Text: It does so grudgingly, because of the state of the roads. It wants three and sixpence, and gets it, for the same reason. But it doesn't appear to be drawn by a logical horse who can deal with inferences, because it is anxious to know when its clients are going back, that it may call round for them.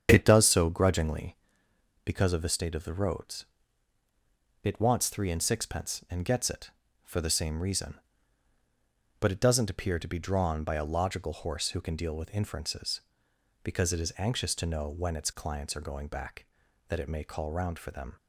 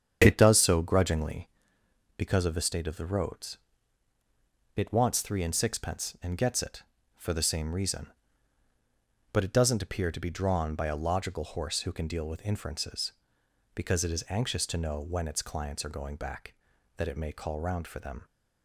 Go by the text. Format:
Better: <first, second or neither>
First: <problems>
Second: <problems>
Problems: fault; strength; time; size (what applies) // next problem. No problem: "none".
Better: neither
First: starts louder than the rest; strong; until 1.1 s; 8 dB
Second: starts louder than the rest; strong; until 1.2 s; 8 dB